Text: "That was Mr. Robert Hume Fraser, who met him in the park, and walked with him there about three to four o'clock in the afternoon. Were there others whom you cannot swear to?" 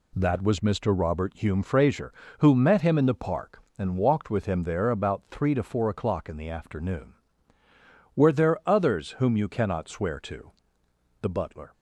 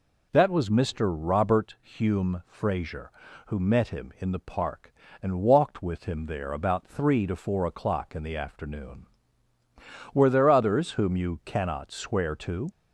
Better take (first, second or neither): second